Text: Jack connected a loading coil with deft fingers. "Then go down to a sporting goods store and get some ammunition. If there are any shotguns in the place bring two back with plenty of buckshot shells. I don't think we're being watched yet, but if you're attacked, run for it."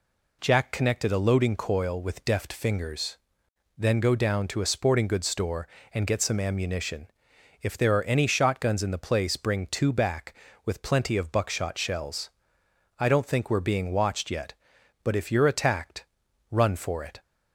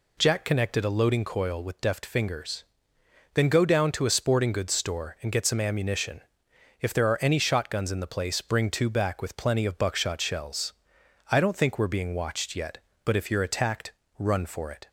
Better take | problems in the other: neither | none

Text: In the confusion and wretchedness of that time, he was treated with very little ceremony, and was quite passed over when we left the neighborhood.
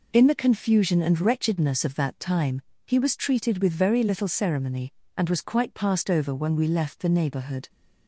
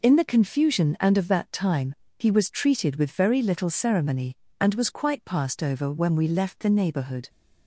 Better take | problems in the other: first | skips "wretchedness"; at 1.1 s

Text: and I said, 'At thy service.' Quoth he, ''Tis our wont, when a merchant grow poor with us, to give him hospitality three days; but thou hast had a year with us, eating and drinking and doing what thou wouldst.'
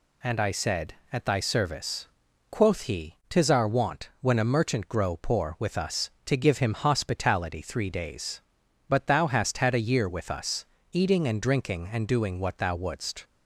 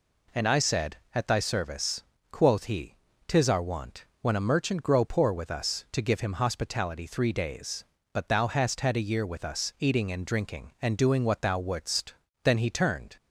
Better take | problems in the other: first | goes on to say "Then he turned"; noticeable; from 12.4 s on; 0.72 s long

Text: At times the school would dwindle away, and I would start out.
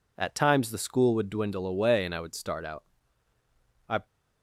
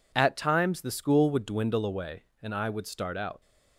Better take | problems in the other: second | goes on to say "I"; slight; from 3.8 s on; 0.18 s long

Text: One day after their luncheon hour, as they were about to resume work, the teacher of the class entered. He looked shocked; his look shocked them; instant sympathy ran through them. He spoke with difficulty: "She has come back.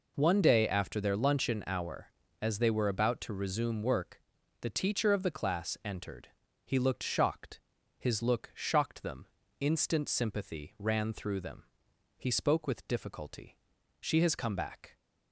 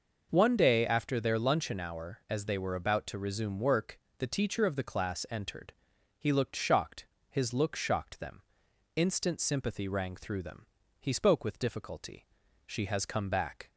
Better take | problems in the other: first | says "rang" for "ran"; at 9.8 s

